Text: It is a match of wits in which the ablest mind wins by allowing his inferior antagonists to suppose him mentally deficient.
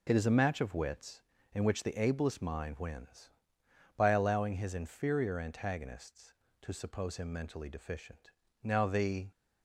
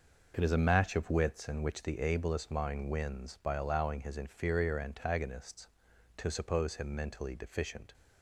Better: second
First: goes on to say "Now the"; noticeable; from 8.6 s on; 0.64 s long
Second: none

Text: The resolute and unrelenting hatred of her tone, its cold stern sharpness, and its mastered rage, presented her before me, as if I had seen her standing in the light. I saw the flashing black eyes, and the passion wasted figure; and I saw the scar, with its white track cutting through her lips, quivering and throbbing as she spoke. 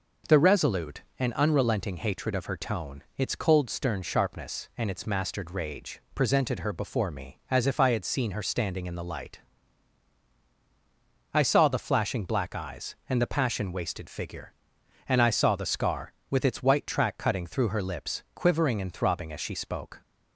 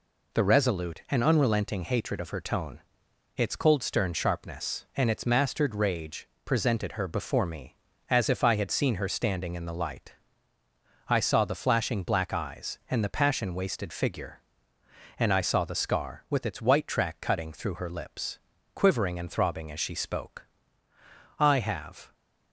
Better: first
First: none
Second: goes on to say "I have"; noticeable; from 21.3 s on; 0.74 s long

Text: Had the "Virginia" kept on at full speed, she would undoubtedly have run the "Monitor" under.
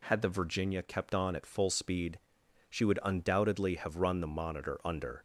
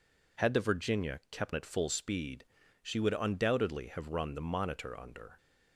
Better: first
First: none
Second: skips "on"; at 1.5 s

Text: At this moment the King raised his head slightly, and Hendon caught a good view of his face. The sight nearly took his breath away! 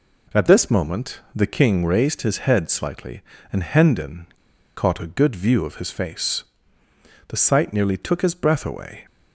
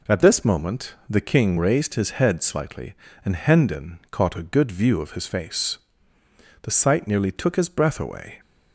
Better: second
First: pauses between "Hendon" and "caught"; noticeable; at 4.2 s; 0.48 s long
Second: none

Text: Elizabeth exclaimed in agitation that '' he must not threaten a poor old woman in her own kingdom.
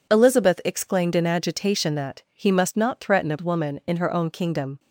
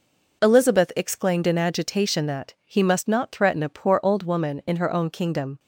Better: second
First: skips "poor old"; at 3.3 s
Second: none

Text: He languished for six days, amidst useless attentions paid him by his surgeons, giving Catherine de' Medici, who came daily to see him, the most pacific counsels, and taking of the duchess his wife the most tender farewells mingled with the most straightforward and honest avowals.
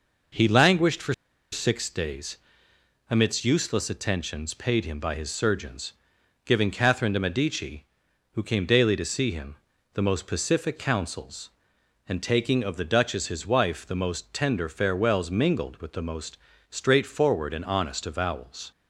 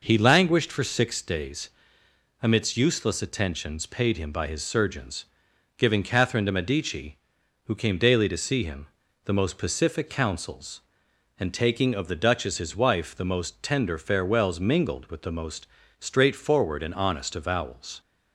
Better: second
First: pauses between "for" and "six"; at 1.1 s; 0.38 s long // pauses between "most" and "straightforward"; slight; at 16.3 s; 0.34 s long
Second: pauses between "most" and "straightforward"; slight; at 15.6 s; 0.34 s long

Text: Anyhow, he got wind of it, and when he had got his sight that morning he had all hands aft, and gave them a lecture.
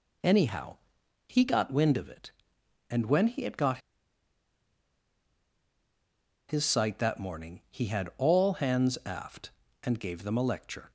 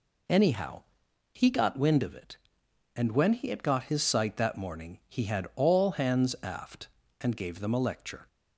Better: second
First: pauses between "got" and "his"; strong; at 3.7 s; 2.7 s long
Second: none

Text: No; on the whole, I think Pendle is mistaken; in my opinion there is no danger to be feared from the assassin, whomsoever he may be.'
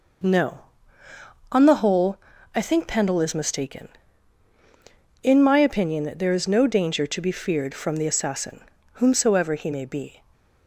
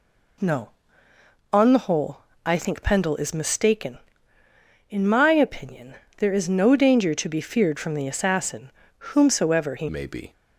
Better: first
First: none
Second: pauses between "opinion" and "there"; slight; at 5.9 s; 0.22 s long // changes voice at "may"; from 9.8 s on; 0.5 s long

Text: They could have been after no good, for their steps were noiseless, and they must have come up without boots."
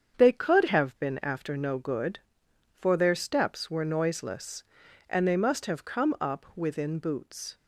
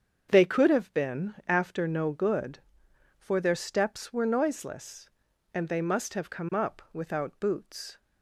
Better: second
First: starts louder than the rest; strong; until 1.2 s; 7.5 dB // says "within" for "without"; at 6.5 s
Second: starts louder than the rest; strong; until 1.3 s; 7 dB

